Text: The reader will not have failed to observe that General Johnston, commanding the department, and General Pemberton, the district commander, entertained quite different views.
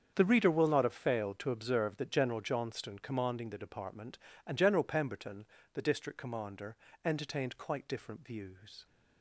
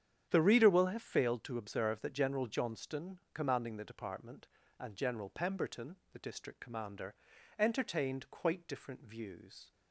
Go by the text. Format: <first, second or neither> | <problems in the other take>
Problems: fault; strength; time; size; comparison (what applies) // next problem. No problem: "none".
first | starts louder than the rest; strong; until 1.3 s; 9 dB; strong in the first // skips "not"; at 0.8 s